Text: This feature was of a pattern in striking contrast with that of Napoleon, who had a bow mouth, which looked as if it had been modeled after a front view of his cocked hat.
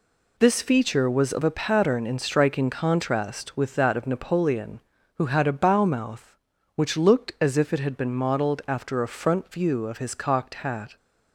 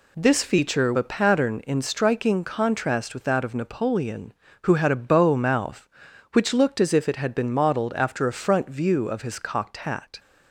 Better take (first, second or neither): first